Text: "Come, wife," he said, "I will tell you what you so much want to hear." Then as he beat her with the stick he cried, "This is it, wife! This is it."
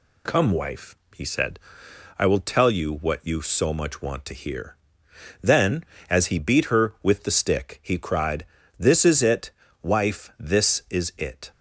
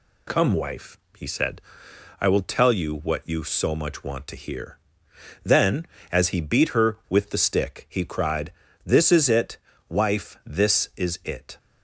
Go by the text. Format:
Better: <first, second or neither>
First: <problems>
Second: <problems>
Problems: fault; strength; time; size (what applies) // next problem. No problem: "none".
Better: neither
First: none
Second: none